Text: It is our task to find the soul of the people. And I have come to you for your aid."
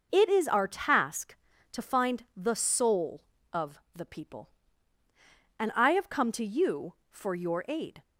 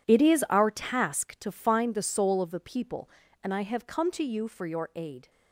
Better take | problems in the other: first | gets quieter; strong; throughout; 14 dB

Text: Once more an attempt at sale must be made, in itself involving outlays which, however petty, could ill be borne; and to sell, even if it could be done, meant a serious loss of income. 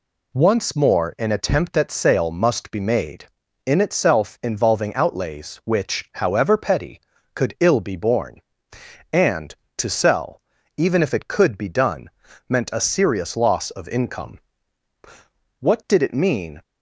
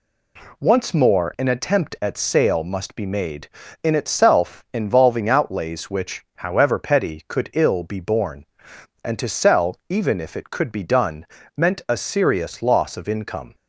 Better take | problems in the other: second | goes on to say "What did it mean"; noticeable; from 15.6 s on; 1.0 s long

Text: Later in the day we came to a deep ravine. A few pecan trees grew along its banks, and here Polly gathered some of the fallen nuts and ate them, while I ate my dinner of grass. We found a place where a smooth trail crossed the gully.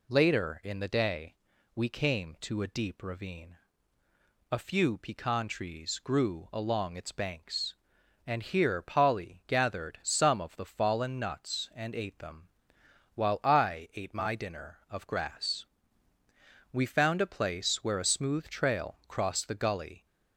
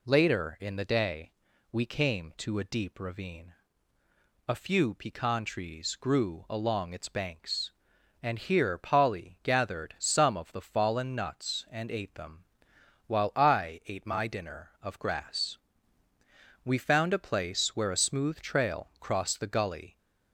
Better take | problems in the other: neither | pauses between "day" and "we"; the same in both

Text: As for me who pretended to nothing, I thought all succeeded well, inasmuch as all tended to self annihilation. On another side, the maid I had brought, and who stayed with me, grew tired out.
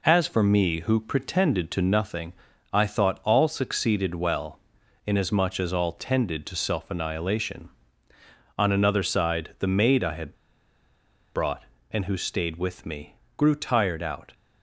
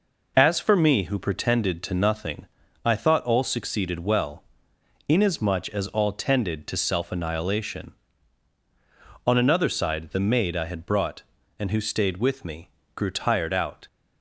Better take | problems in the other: second | pauses between "had" and "brought"; at 10.3 s; 1.0 s long

